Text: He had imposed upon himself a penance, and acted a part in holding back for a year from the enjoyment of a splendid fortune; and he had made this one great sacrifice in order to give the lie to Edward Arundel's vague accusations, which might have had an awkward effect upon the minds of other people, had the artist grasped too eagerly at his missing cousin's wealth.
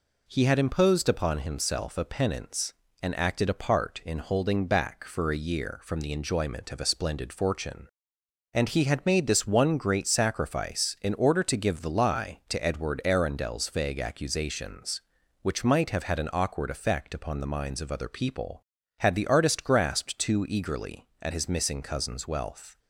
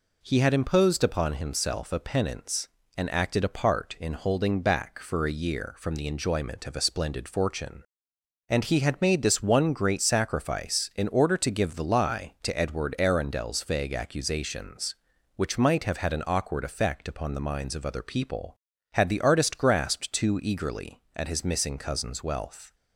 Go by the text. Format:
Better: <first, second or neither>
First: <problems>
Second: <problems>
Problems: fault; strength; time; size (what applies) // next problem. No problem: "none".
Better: neither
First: none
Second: none